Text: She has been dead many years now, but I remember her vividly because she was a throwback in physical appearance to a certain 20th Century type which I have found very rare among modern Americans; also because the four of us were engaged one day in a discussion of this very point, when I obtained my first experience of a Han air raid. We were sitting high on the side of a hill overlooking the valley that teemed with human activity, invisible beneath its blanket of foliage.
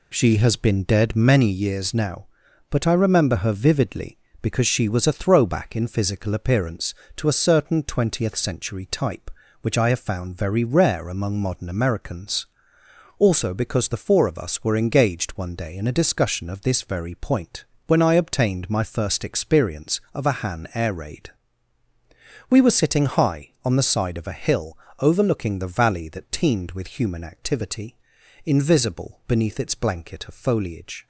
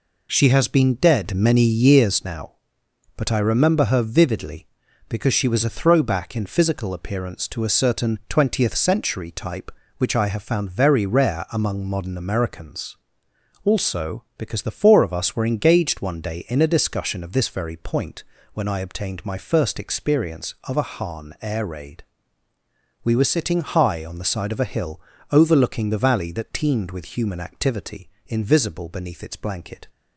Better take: first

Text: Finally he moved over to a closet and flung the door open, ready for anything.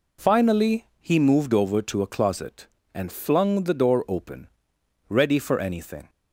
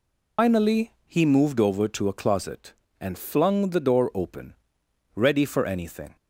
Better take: first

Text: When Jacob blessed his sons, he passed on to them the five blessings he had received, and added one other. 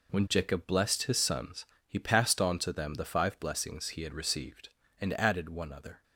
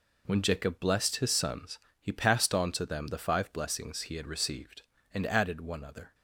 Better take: neither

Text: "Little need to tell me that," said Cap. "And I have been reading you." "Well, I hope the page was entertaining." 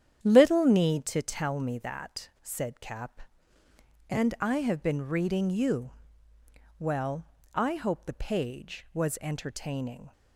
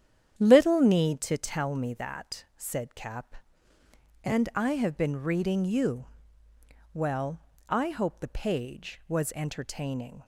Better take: neither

